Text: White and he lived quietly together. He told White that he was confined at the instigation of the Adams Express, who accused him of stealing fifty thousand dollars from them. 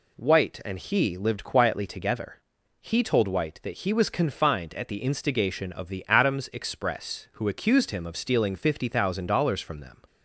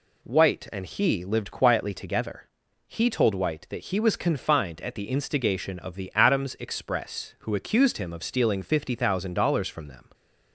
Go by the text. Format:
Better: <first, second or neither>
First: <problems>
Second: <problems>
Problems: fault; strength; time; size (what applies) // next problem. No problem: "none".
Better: neither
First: none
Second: none